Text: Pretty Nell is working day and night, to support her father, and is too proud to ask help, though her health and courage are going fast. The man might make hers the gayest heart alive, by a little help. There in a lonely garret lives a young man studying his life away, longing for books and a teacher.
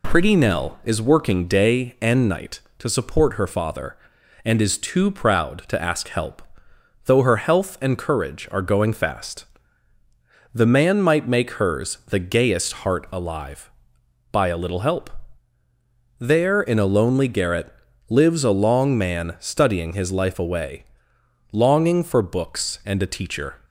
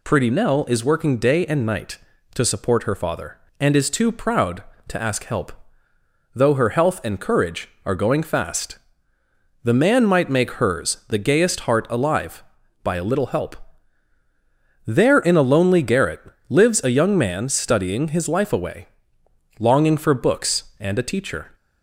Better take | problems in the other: second | pauses between "garret" and "lives"; slight; at 17.7 s; 0.34 s long; slight in the second // says "long" for "young"; at 18.5 s

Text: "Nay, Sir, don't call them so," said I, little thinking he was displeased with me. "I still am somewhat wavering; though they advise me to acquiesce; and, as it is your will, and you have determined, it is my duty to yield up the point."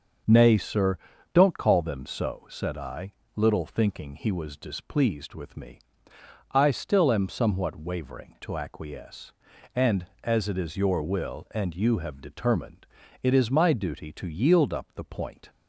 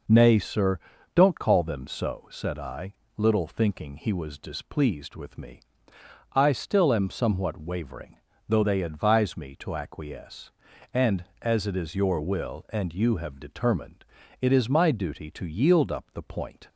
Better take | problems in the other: second | starts louder than the rest; until 1.6 s; 6.5 dB // skips "though they advise me"; at 8.3 s

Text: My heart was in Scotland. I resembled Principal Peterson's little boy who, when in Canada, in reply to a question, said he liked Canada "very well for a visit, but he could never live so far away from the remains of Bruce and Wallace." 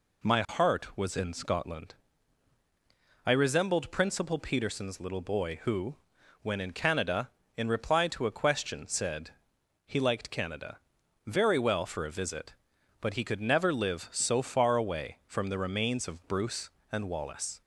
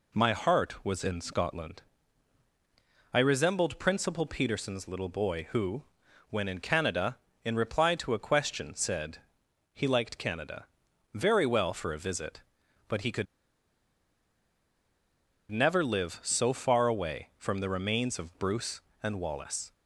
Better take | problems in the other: first | pauses between "said" and "he"; noticeable; at 9.1 s; 0.54 s long; noticeable in the first // pauses between "Canada" and "very"; noticeable; at 10.6 s; 0.48 s long; noticeable in the first // pauses between "could" and "never"; strong; at 13.2 s; 2.2 s long

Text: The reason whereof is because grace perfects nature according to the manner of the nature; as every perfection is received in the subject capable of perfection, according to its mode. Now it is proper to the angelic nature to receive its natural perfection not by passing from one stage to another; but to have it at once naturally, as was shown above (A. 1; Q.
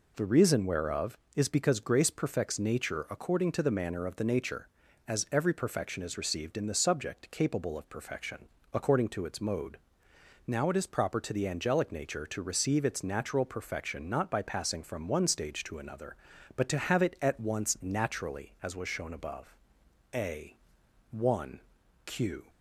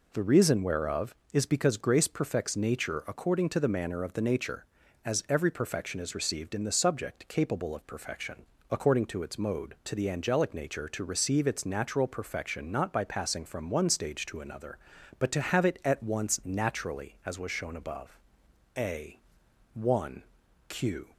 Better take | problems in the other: first | skips "Now it is proper"; at 9.8 s

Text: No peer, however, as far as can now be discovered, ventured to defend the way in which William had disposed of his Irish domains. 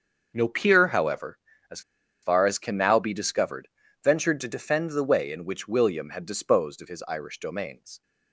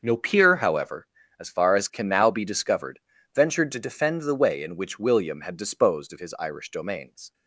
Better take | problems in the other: second | starts louder than the rest; until 1.3 s; 6.5 dB; also in the second // pauses between "as" and "far"; at 1.8 s; 0.41 s long

